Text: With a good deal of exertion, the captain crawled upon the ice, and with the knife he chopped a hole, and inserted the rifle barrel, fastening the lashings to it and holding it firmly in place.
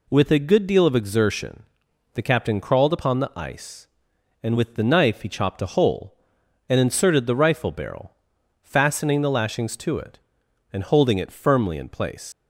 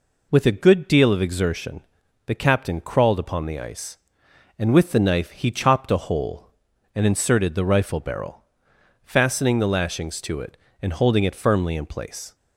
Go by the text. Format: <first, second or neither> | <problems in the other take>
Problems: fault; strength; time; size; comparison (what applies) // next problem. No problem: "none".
second | leaves "place" unfinished; at 12.3 s; 175 ms